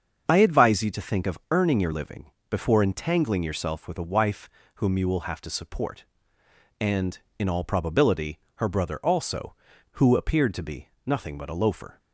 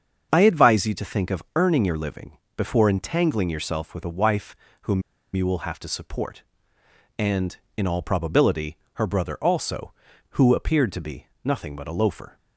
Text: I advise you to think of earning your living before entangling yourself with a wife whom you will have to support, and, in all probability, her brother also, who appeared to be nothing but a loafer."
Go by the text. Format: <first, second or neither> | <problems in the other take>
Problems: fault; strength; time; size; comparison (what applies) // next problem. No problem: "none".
first | starts louder than the rest; until 1.3 s; 7 dB; also in the first // pauses between "living" and "before"; slight; at 2.3 s; 0.18 s long; slight in the first // pauses between "wife" and "whom"; slight; at 4.5 s; 0.26 s long; slight in the first // pauses between "whom" and "you"; slight; at 5.0 s; 0.33 s long // pauses between "be" and "nothing"; slight; at 11.2 s; 0.18 s long; slight in the first